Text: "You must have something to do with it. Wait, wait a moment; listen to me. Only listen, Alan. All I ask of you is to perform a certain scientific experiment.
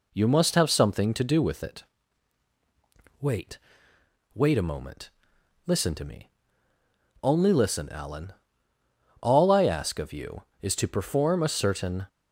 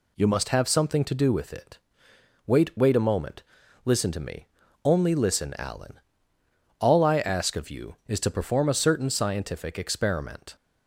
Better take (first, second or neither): second